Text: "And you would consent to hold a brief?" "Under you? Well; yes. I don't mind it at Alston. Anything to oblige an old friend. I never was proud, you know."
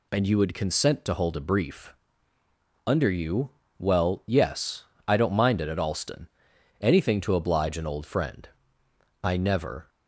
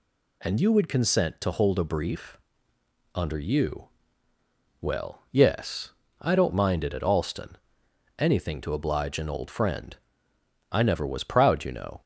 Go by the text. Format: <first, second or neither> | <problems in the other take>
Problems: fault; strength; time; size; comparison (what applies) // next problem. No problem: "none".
second | stops before "was proud you know"; at 9.8 s